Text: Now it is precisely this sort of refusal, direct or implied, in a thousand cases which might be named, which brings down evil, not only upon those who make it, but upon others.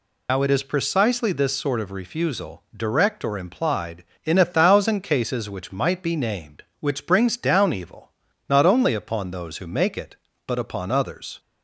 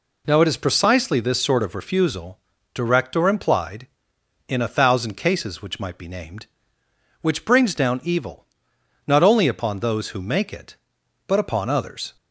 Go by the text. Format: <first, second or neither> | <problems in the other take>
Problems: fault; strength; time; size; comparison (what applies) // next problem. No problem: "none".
second | loses the start of "Now"; at 0.2 s; 120 ms